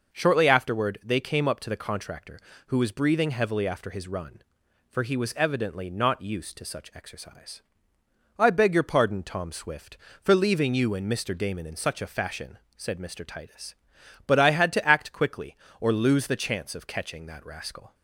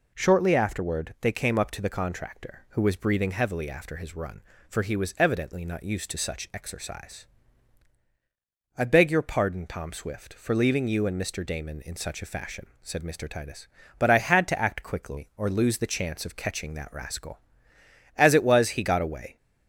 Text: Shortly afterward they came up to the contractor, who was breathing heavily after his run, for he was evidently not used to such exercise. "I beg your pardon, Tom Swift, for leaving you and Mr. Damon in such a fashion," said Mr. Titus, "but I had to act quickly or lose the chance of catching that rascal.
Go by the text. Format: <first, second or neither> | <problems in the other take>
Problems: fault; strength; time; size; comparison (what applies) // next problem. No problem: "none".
first | goes on to say "As it was he got away"; noticeable; from 18.1 s on; 1.2 s long